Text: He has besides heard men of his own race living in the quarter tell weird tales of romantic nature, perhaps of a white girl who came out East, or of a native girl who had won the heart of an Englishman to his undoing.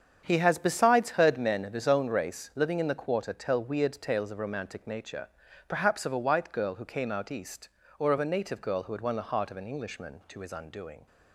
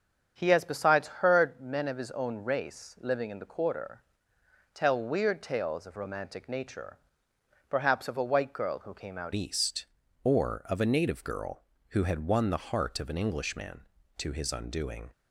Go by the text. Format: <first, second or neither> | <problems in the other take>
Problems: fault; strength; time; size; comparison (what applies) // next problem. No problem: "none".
first | starts louder than the rest; strong; until 1.3 s; 7.5 dB; strong in the first // pauses between "quarter" and "tell"; noticeable; at 4.0 s; 0.72 s long // changes voice at "East"; from 9.3 s on; 5.8 s long